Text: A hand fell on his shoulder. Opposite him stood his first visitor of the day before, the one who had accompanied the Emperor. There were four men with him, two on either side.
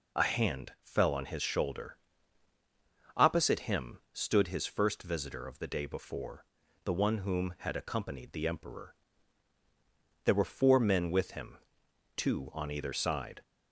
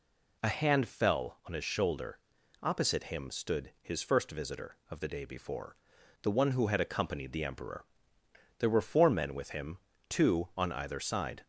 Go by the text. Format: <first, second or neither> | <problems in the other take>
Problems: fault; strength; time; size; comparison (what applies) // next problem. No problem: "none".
second | says "whom" for "who"; at 7.1 s